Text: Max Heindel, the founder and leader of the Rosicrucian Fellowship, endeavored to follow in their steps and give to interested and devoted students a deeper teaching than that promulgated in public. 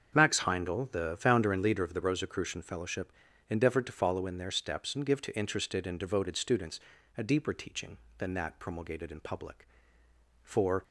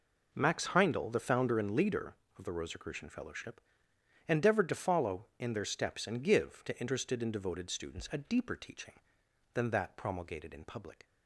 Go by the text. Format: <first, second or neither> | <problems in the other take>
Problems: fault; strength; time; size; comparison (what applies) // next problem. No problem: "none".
second | starts louder than the rest; until 1.1 s; 7 dB // pauses between "students" and "a"; at 6.7 s; 0.38 s long // goes on to say "For"; slight; from 10.4 s on; 0.40 s long